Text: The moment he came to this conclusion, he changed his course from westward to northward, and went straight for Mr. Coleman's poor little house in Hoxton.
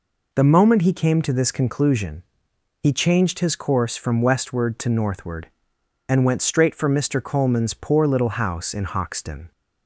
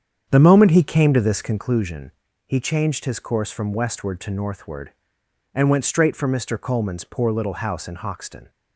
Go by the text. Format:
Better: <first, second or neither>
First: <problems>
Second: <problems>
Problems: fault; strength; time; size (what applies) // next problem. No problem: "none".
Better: first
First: none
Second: starts louder than the rest; strong; until 1.8 s; 8 dB